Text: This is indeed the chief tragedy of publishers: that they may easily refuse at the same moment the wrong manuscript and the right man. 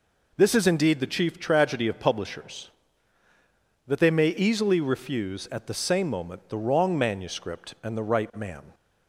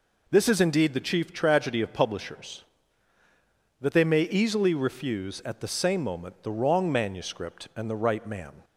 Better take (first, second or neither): neither